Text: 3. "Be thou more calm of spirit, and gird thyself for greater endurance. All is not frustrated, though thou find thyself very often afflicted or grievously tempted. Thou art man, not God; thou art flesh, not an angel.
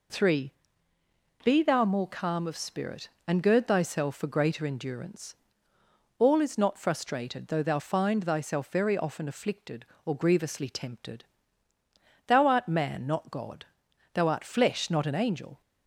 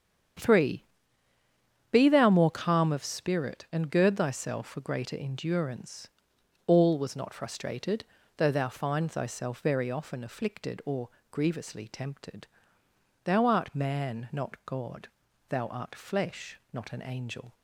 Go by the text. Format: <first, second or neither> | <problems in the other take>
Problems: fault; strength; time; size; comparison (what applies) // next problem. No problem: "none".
first | starts louder than the rest; strong; until 2.4 s; 8.5 dB // says "was" for "is"; at 6.9 s // pauses between "or" and "grievously"; slight; at 11.0 s; 0.22 s long